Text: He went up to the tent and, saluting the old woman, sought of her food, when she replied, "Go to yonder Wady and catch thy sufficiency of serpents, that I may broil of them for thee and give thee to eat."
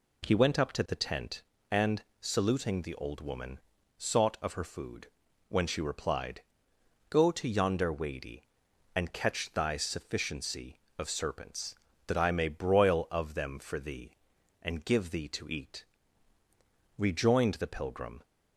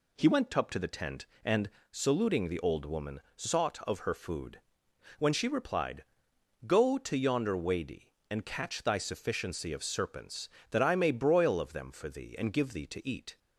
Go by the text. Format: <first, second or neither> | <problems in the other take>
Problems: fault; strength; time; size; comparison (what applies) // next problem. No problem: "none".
second | goes on to say "Rejoined the pilgrim"; noticeable; from 16.9 s on; 1.2 s long